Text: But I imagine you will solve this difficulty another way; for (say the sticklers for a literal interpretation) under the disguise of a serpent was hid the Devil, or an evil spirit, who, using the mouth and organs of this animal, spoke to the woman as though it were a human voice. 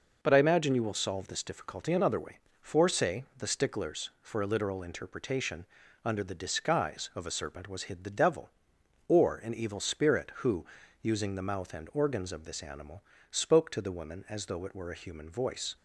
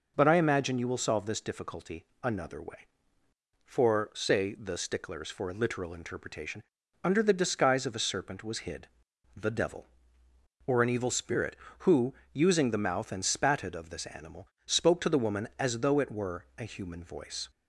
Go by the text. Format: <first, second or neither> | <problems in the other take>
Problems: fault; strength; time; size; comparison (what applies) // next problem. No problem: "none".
first | pauses between "difficulty" and "another"; slight; at 2.0 s; 0.18 s long // pauses between "hid" and "the"; noticeable; at 8.8 s; 0.48 s long // says "spatted" for "organs"; at 13.2 s